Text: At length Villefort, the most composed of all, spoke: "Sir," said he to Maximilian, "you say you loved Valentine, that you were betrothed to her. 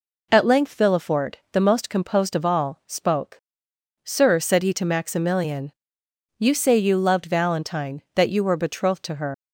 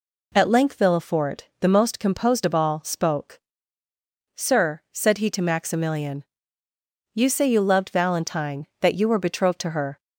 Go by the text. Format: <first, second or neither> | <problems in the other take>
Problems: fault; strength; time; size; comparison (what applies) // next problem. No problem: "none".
second | leaves "her" unfinished; at 9.3 s; 110 ms